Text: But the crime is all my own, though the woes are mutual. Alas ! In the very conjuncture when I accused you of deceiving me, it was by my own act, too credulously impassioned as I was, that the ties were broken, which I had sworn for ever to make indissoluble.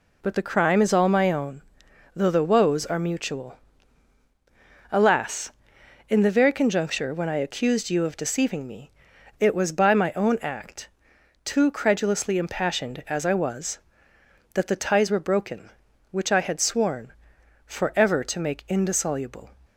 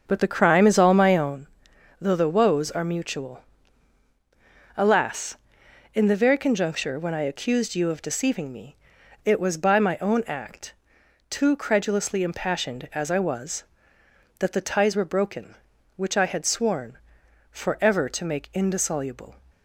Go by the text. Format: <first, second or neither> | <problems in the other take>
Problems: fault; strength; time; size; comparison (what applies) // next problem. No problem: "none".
first | starts louder than the rest; until 1.5 s; 7 dB